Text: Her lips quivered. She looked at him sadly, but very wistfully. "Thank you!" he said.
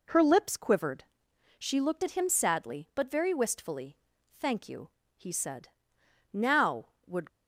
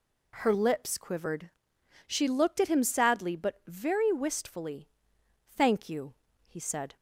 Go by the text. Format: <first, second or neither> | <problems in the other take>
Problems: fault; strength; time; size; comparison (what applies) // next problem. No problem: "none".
second | goes on to say "Now would"; noticeable; from 6.3 s on; 0.94 s long